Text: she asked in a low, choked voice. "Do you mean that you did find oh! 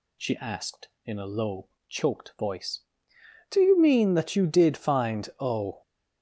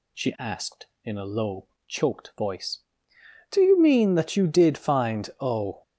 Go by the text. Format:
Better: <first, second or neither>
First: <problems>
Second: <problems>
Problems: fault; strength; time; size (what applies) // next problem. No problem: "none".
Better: neither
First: none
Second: none